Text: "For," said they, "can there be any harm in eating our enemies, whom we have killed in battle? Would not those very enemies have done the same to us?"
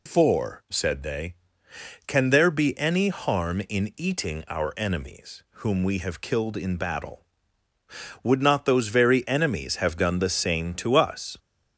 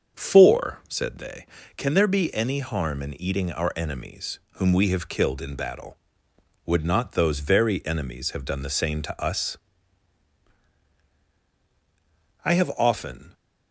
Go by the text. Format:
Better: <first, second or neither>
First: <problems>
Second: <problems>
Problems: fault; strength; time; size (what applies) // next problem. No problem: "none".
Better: first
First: none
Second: starts louder than the rest; until 1.2 s; 7 dB // goes on to say "I have often"; noticeable; from 12.4 s on; 0.88 s long